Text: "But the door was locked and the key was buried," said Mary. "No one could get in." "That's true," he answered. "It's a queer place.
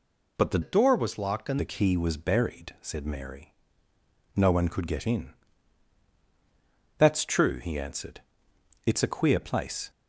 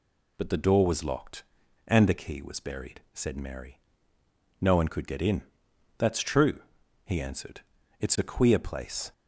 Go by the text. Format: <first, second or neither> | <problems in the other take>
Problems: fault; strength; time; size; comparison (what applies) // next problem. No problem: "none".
second | changes voice from "door" to "and"; from 0.6 to 1.5 s; 0.9 s long